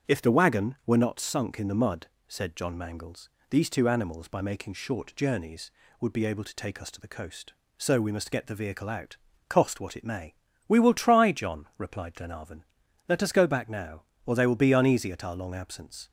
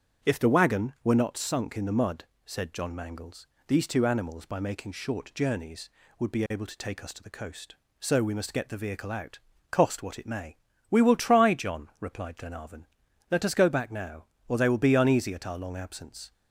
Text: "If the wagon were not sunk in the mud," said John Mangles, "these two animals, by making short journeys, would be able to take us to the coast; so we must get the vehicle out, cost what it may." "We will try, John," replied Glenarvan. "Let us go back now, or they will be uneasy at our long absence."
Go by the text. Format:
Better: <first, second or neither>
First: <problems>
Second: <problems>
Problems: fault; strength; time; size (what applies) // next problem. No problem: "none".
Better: neither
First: starts louder than the rest; strong; until 1.1 s; 8 dB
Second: starts louder than the rest; strong; until 1.3 s; 8 dB